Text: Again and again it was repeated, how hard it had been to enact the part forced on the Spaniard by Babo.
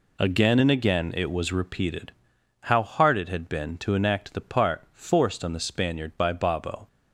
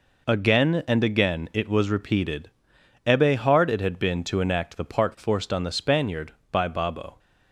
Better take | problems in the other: first | says "ebbe" for "how"; at 3.0 s

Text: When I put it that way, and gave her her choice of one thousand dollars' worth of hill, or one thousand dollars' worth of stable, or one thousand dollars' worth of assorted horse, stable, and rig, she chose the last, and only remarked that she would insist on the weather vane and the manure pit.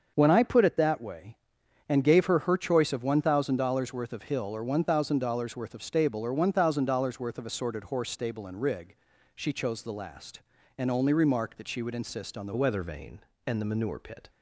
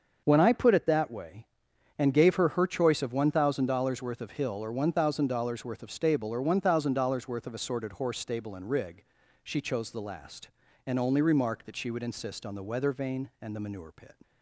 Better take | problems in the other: second | starts louder than the rest; until 1.1 s; 6.5 dB; also in the second // changes voice at "weather"; from 12.5 s on; 1.7 s long

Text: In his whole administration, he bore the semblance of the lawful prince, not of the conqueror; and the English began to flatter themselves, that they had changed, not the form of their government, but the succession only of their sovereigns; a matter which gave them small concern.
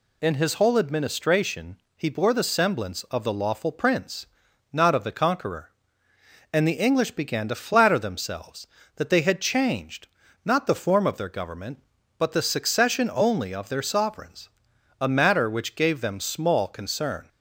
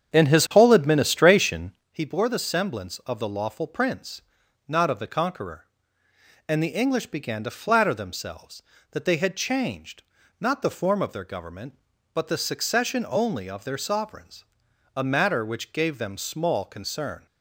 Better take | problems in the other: first | starts louder than the rest; strong; until 1.8 s; 8 dB

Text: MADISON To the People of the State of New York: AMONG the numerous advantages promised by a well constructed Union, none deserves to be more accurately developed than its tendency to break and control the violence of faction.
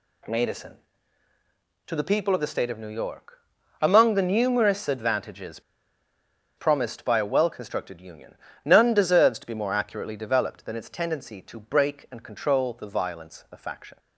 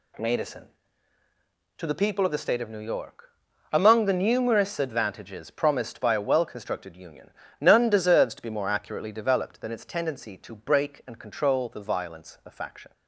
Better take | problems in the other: second | pauses between "advantages" and "promised"; noticeable; at 5.5 s; 0.97 s long

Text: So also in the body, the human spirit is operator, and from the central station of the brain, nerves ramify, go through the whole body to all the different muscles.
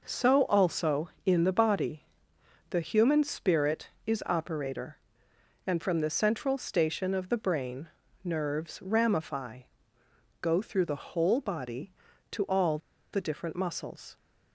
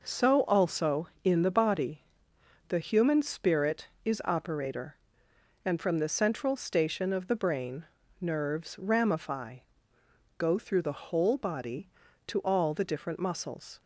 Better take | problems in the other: second | pauses between "all" and "the"; slight; at 12.7 s; 0.35 s long

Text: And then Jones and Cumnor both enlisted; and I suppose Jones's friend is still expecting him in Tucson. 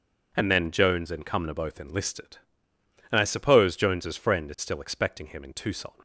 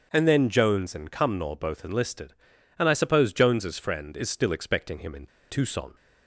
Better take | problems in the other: first | starts louder than the rest; strong; until 1.1 s; 7 dB // pauses between "in" and "Tucson"; slight; at 5.2 s; 0.23 s long

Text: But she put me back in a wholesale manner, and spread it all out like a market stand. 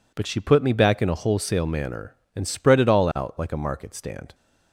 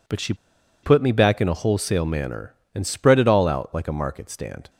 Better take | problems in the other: first | pauses between "she" and "put"; noticeable; at 0.3 s; 0.48 s long

